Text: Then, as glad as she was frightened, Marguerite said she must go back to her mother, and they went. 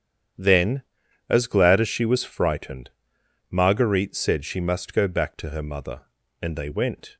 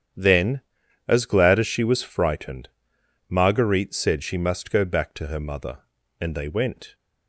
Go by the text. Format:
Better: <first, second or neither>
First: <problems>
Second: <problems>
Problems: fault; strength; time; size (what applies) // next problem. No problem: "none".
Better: neither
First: starts louder than the rest; strong; until 1.8 s; 9 dB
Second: starts louder than the rest; strong; until 1.6 s; 9 dB